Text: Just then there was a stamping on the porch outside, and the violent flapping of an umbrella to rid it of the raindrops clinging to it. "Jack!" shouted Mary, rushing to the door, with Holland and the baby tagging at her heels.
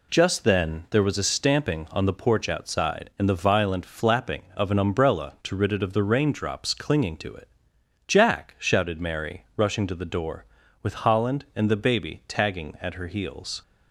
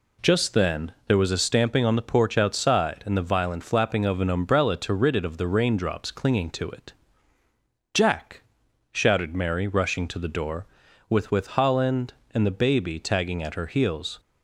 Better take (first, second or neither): first